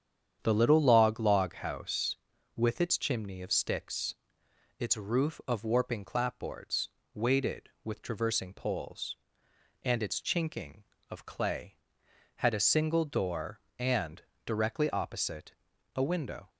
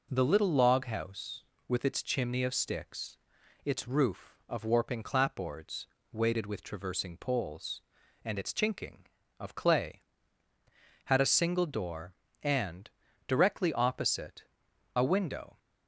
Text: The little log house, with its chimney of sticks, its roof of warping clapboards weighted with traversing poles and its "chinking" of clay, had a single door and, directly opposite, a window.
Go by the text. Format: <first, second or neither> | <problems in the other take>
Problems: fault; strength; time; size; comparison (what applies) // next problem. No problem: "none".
second | starts louder than the rest; strong; until 1.4 s; 8.5 dB // says "log" twice; at 1.1 s // pauses between "clapboards" and "weighted"; slight; at 6.8 s; 0.22 s long; slight in the second